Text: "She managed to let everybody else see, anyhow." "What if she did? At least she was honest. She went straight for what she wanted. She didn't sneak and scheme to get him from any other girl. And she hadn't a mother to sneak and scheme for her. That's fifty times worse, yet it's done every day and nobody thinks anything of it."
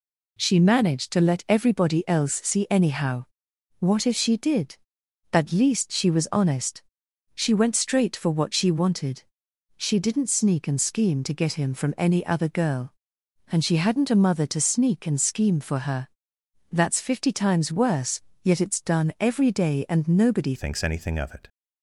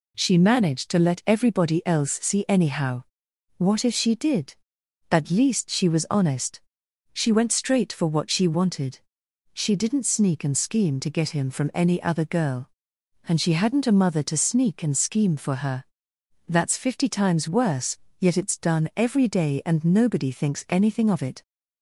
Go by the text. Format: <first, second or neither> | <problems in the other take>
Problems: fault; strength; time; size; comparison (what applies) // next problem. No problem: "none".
second | changes voice at "thinks"; from 20.5 s on; 0.9 s long